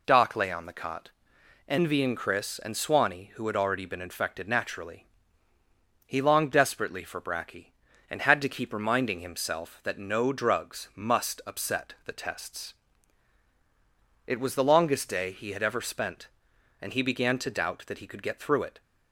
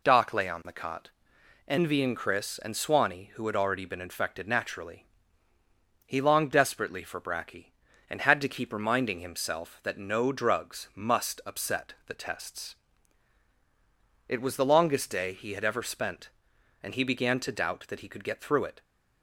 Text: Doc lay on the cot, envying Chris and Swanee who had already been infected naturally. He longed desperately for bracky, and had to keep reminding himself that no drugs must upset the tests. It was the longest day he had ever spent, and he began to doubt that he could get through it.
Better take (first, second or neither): neither